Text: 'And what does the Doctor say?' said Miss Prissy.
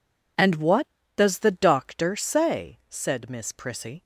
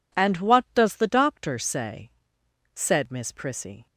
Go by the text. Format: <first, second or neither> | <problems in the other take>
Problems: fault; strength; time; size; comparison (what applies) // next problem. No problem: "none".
neither | none